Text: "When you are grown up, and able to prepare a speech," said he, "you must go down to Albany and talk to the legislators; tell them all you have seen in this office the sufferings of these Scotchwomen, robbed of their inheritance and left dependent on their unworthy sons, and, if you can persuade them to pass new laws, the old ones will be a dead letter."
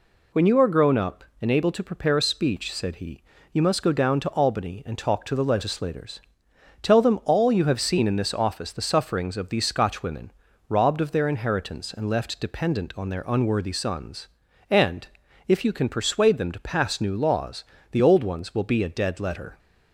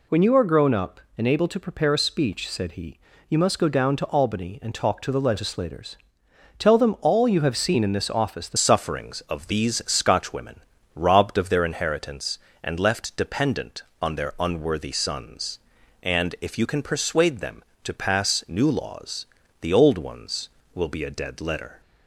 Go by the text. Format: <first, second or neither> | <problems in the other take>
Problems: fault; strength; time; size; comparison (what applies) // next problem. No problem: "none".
first | changes voice at "sufferings"; from 8.5 s on; 13.3 s long